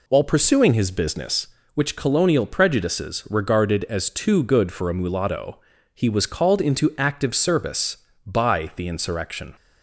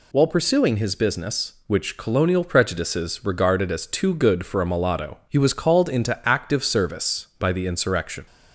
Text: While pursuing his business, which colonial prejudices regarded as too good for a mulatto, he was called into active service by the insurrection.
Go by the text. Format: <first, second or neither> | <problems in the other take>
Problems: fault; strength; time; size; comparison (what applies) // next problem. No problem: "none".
second | starts louder than the rest; slight; until 1.7 s; 3 dB